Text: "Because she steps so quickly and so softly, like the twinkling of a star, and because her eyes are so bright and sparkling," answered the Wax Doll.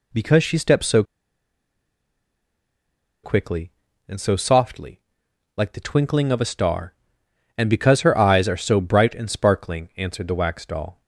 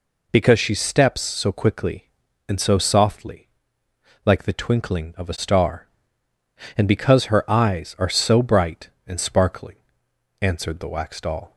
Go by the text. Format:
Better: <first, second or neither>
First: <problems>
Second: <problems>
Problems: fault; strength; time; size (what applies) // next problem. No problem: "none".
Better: second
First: pauses between "so" and "quickly"; strong; at 1.0 s; 2.2 s long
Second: none